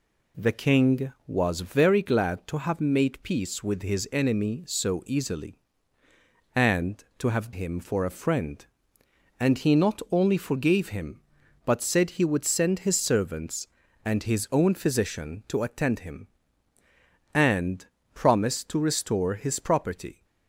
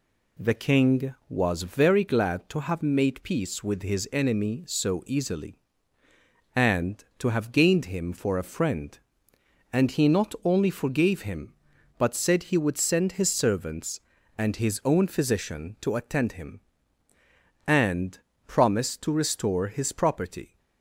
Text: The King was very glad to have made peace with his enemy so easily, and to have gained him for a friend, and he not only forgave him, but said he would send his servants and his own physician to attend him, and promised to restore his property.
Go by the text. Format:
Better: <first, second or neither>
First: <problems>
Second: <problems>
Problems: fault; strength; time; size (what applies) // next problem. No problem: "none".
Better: second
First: skips "gained"; at 7.5 s // pauses between "and" and "promised"; slight; at 17.8 s; 0.26 s long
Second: pauses between "and" and "promised"; slight; at 18.1 s; 0.26 s long